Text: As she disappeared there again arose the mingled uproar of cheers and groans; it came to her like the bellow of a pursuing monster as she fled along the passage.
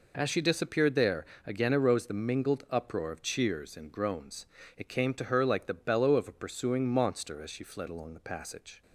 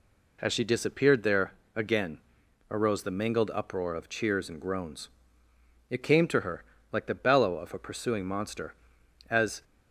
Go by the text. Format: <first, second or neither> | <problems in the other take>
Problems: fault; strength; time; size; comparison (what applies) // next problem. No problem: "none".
first | pauses between "there" and "again"; slight; at 1.5 s; 0.24 s long; slight in the first // pauses between "again" and "arose"; noticeable; at 2.1 s; 0.54 s long // pauses between "her" and "like"; slight; at 6.6 s; 0.30 s long // stops before "she fled along the passage"; at 9.6 s